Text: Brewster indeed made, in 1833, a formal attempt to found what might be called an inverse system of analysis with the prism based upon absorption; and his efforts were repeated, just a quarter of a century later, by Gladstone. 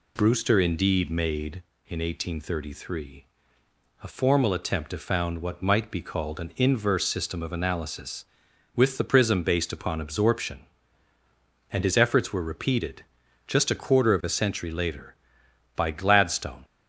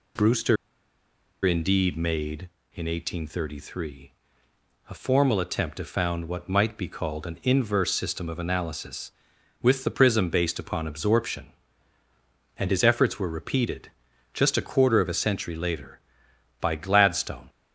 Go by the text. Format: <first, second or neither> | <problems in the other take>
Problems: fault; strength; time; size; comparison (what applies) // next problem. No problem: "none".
first | pauses between "Brewster" and "indeed"; noticeable; at 0.5 s; 0.89 s long